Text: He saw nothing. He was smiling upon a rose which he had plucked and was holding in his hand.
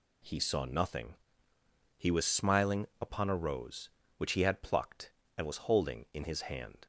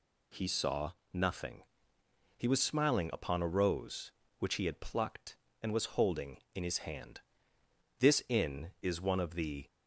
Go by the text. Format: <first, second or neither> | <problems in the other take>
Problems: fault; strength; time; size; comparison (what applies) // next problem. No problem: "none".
first | pauses between "saw" and "nothing"; slight; at 0.9 s; 0.20 s long // goes on to say "This inn is one of the"; strong; from 7.9 s on; 1.6 s long